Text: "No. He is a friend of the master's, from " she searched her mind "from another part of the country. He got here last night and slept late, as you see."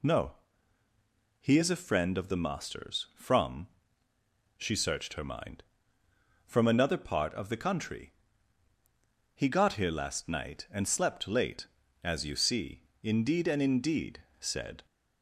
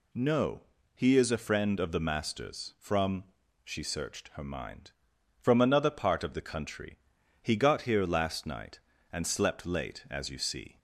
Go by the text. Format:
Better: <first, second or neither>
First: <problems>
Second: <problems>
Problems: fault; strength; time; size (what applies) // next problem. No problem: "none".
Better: second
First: goes on to say "Indeed and indeed said"; strong; from 13.0 s on; 1.8 s long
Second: none